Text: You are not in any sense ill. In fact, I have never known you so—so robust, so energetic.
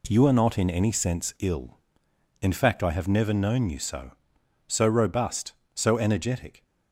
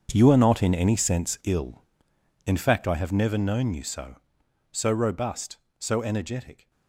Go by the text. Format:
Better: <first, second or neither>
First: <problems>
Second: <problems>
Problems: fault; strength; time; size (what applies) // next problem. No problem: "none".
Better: first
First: none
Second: gets quieter; strong; throughout; 14.5 dB